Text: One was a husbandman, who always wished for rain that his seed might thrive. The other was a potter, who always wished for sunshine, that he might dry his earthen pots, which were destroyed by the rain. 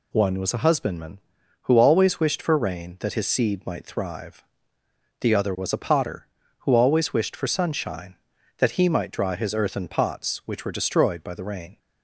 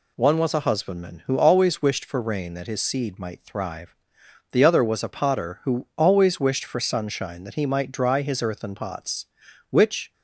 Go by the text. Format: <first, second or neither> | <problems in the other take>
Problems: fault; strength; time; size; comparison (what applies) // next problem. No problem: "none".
first | stops before "were destroyed by the rain"; at 10.1 s